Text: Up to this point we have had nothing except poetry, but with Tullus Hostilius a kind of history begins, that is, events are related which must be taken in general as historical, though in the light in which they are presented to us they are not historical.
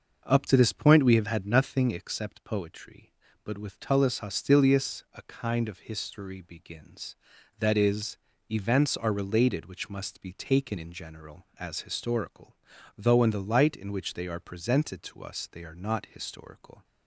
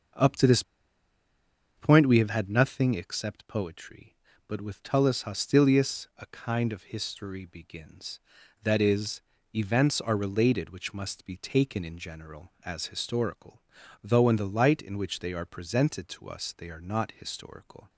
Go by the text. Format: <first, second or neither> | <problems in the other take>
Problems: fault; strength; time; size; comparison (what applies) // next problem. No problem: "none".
first | pauses between "this" and "point"; at 0.6 s; 1.1 s long